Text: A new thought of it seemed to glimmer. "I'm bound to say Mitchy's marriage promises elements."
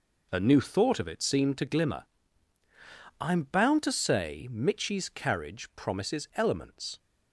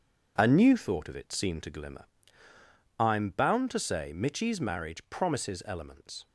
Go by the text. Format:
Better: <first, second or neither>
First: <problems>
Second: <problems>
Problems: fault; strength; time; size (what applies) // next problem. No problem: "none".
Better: second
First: says "carriage" for "marriage"; at 5.0 s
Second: none